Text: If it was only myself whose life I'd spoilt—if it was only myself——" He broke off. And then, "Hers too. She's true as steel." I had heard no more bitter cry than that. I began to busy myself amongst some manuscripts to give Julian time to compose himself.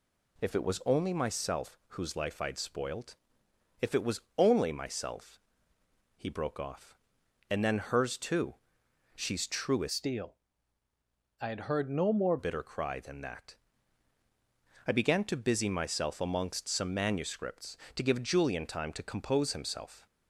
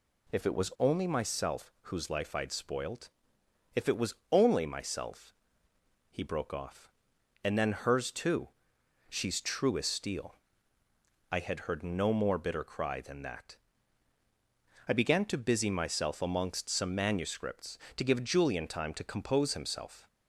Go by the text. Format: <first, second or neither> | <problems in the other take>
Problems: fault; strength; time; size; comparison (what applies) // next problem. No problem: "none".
second | pauses between "was" and "only"; slight; at 4.2 s; 0.16 s long; slight in the second // changes voice from "steel" to "more"; from 9.8 to 12.3 s; 2.5 s long